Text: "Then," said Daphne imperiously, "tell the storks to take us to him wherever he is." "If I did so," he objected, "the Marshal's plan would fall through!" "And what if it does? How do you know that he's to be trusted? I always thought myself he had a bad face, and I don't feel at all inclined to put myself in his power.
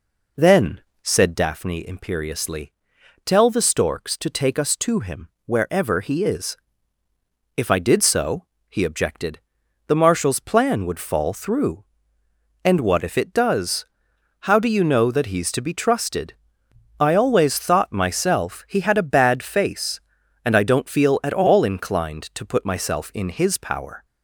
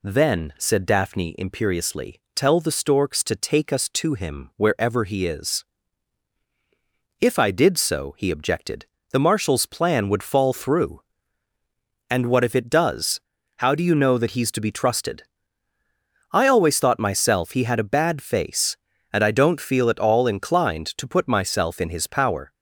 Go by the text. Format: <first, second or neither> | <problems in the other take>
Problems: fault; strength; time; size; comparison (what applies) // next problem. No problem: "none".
second | starts louder than the rest; until 1.5 s; 4 dB // pauses between "him" and "wherever"; slight; at 5.2 s; 0.16 s long